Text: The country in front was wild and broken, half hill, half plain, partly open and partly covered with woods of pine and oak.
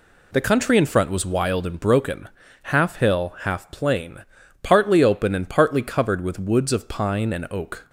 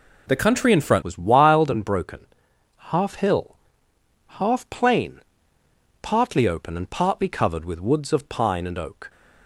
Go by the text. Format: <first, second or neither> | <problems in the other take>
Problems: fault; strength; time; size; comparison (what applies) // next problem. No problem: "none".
first | changes voice at "was"; from 1.0 s on; 8.0 s long